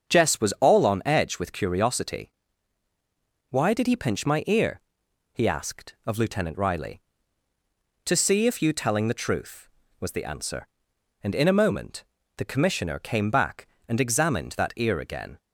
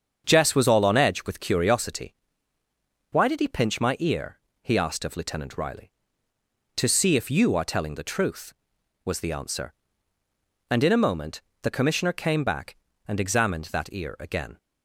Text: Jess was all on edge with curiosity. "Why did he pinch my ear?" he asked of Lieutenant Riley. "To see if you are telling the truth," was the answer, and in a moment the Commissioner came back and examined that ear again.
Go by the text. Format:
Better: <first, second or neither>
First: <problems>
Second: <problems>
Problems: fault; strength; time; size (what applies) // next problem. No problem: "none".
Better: second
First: starts louder than the rest; strong; until 1.2 s; 7.5 dB // skips "are"; at 8.7 s // pauses between "moment" and "the"; slight; at 12.0 s; 0.32 s long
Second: starts louder than the rest; strong; until 1.3 s; 7 dB // pauses between "moment" and "the"; slight; at 11.4 s; 0.20 s long